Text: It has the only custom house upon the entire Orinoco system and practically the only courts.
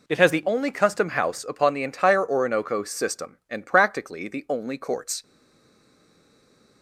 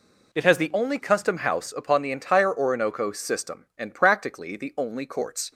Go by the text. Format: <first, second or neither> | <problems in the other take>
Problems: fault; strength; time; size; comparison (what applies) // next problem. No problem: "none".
second | stays silent after the last word; noticeable; from 5.2 s on; 1.6 s long